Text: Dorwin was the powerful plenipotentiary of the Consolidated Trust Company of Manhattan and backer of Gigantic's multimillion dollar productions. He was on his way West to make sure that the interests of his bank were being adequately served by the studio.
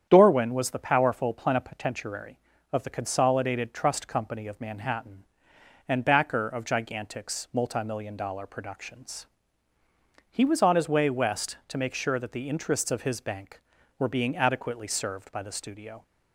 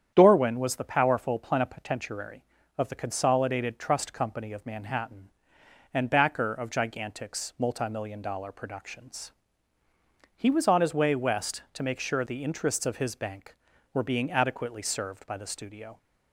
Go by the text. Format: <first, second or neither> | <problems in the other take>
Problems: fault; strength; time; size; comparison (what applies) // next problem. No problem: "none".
first | starts louder than the rest; strong; until 1.1 s; 9 dB; strong in the first // skips "that"; at 12.2 s